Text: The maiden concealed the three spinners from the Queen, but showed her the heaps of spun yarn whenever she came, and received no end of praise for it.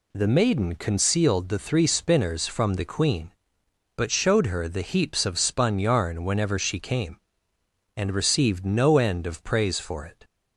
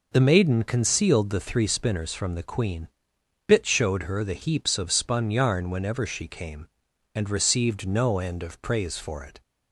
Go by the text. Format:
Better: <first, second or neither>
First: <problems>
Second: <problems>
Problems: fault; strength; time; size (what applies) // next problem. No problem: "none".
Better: first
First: none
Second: says "bit" for "but"; at 3.4 s